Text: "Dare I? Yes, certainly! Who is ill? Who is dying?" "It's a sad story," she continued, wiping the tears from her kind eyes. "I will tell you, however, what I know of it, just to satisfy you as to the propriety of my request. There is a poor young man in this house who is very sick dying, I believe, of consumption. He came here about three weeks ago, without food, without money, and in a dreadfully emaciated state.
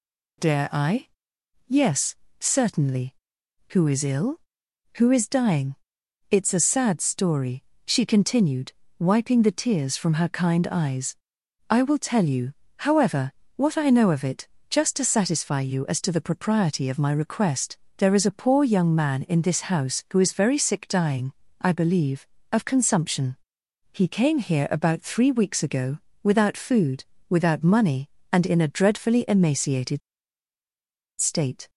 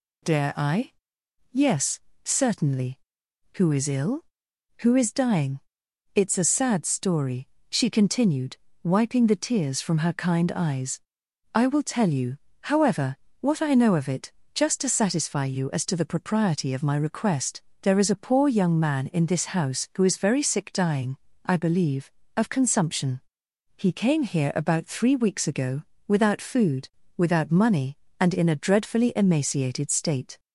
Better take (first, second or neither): second